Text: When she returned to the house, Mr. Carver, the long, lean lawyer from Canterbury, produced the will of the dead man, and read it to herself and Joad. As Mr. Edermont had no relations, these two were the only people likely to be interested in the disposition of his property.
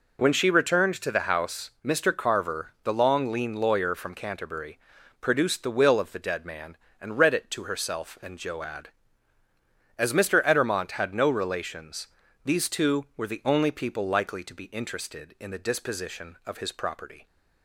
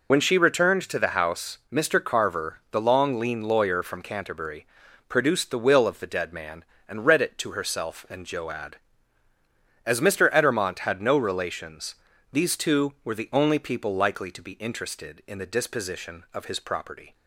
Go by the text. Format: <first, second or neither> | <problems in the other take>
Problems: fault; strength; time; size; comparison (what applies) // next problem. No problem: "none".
first | loses the start of "When"; at 0.1 s; 35 ms